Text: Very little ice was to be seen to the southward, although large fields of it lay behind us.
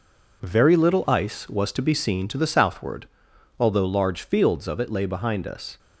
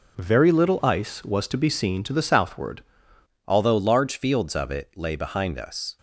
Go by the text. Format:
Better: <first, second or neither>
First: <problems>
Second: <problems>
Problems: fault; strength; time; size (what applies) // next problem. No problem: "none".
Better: first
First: none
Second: changes voice at "although"; from 3.4 s on; 2.5 s long